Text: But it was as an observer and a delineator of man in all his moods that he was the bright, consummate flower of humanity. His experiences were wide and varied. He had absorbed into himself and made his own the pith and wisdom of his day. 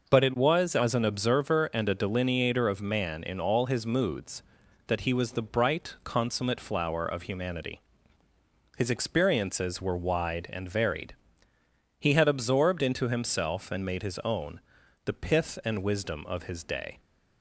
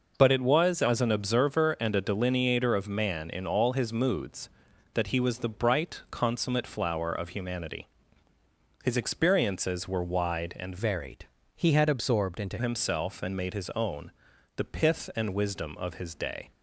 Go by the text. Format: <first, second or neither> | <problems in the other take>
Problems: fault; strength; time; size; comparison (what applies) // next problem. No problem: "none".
first | changes voice from "varied" to "into"; from 10.7 to 12.5 s; 1.8 s long // pauses between "own" and "the"; at 14.1 s; 0.44 s long; also in the first